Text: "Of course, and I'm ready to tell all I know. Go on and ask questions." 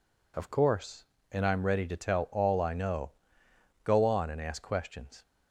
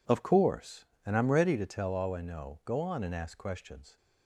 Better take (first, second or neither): neither